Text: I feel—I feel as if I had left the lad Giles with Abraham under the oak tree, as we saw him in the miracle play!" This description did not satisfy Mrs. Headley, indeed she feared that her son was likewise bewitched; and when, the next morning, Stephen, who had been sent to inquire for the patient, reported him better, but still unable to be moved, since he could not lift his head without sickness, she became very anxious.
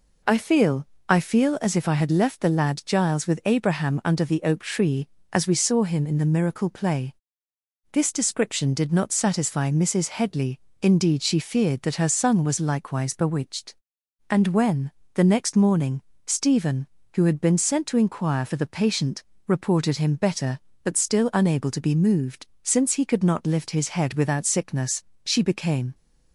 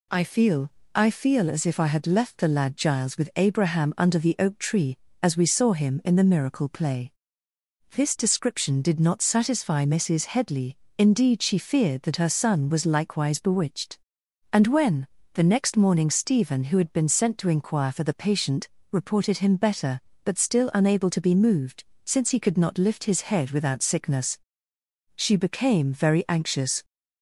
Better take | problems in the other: second | stops before "very anxious"; at 25.9 s

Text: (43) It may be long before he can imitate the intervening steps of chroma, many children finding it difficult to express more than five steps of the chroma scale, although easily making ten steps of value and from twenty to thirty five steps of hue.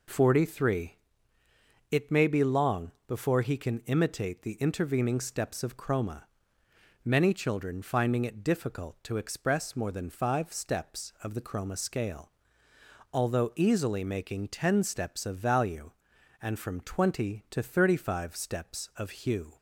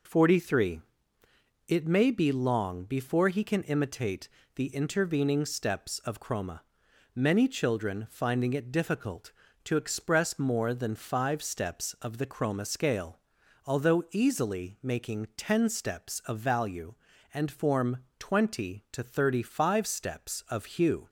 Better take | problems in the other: first | pauses between "imitate" and "the"; slight; at 4.2 s; 0.26 s long // says "form" for "from"; at 17.5 s

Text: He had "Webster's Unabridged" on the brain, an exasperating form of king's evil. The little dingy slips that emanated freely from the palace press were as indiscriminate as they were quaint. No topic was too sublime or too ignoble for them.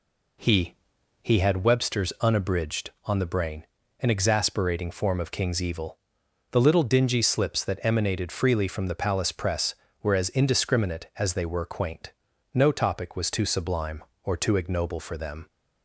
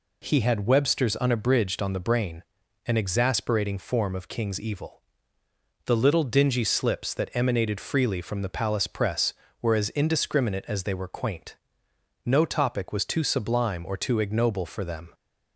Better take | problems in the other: second | says "He" twice; at 1.2 s

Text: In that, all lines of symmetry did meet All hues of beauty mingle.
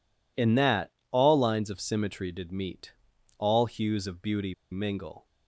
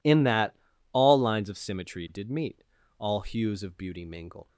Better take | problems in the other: second | pauses between "meet" and "All"; noticeable; at 2.9 s; 0.46 s long; also in the second // pauses between "beauty" and "mingle"; slight; at 4.5 s; 0.18 s long

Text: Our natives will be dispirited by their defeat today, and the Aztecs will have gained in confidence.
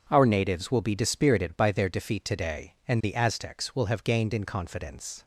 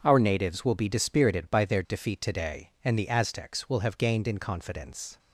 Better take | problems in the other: neither | none

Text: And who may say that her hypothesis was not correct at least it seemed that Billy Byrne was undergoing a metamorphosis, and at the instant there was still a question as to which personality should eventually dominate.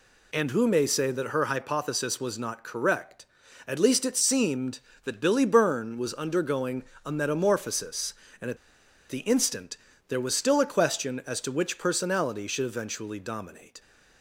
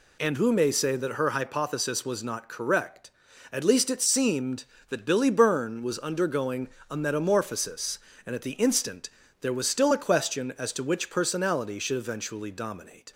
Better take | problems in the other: second | pauses between "undergoing" and "a"; slight; at 6.8 s; 0.20 s long; slight in the second // pauses between "at" and "the"; noticeable; at 8.5 s; 0.53 s long // pauses between "instant" and "there"; slight; at 9.7 s; 0.32 s long; slight in the second

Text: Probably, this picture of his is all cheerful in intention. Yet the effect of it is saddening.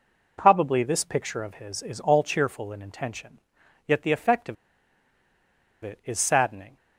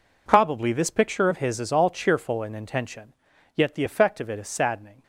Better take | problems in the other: second | pauses between "of" and "it"; strong; at 4.5 s; 1.2 s long

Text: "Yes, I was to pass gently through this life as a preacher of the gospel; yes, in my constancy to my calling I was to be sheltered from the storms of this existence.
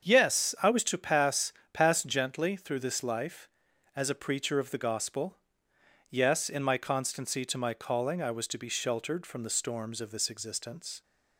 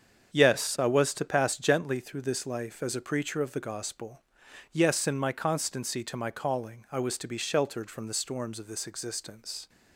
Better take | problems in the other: second | starts louder than the rest; strong; until 1.1 s; 7.5 dB; strong in the second // says "pass" twice; at 1.7 s

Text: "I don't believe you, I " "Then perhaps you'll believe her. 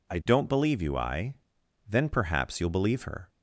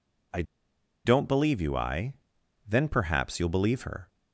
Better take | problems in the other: first | pauses between "I" and "don't"; noticeable; at 0.4 s; 0.64 s long

